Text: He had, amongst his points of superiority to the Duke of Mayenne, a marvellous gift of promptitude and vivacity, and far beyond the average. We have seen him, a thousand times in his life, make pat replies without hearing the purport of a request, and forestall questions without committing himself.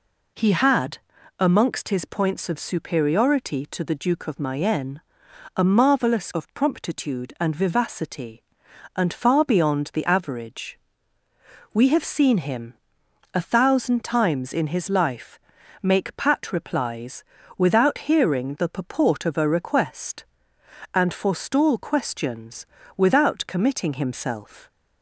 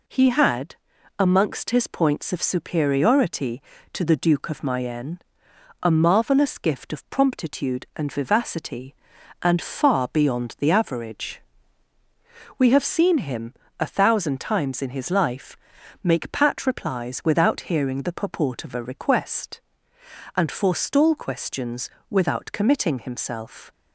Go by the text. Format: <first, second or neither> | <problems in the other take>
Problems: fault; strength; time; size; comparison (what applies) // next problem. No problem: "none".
second | skips "gift"; at 6.3 s // pauses between "replies" and "without"; slight; at 17.2 s; 0.36 s long // pauses between "questions" and "without"; slight; at 22.6 s; 0.30 s long; slight in the second